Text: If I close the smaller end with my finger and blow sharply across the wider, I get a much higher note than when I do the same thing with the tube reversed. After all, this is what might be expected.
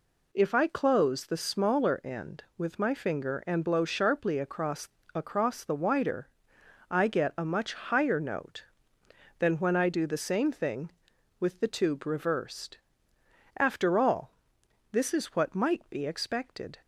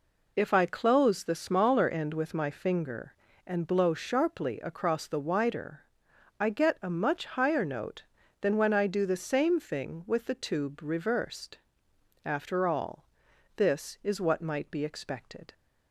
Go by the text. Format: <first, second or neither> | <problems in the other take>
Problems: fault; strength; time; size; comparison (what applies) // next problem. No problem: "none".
second | says "across" twice; at 5.1 s